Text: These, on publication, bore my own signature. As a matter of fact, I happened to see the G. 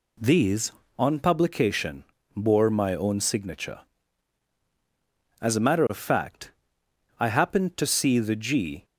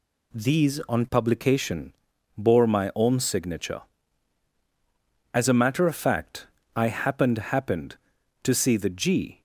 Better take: first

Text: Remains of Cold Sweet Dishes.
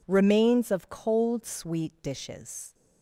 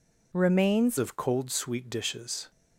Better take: first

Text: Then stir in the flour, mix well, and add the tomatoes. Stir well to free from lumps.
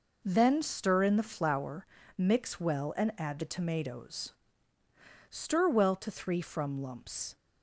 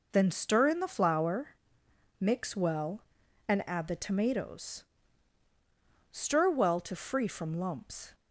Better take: second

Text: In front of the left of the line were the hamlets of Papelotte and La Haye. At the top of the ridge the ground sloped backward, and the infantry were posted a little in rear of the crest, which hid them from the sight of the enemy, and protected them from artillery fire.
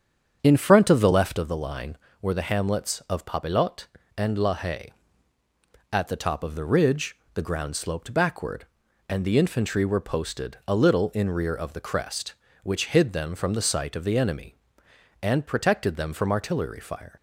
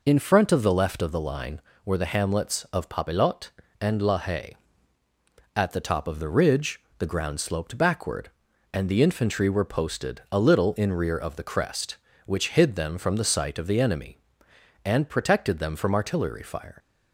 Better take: second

